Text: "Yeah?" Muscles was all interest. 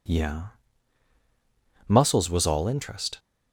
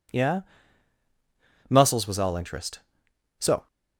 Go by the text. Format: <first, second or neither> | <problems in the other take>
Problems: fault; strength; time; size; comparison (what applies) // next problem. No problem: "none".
first | goes on to say "So"; slight; from 3.3 s on; 0.28 s long